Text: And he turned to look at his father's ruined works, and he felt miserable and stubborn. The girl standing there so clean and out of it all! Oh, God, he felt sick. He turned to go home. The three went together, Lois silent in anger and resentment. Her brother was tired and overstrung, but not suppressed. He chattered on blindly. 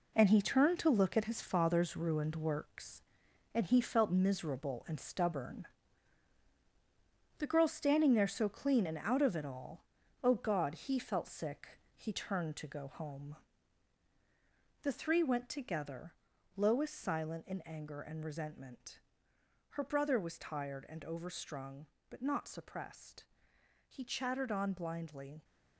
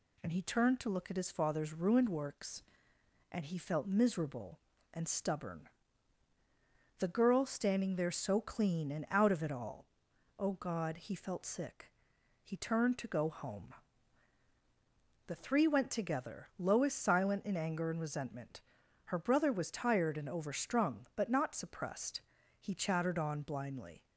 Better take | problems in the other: second | gets quieter; strong; throughout; 8 dB

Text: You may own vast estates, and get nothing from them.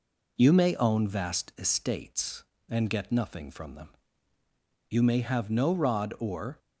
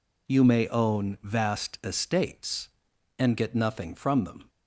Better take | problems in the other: second | goes on to say "You may have no rod or"; strong; from 4.9 s on; 1.6 s long

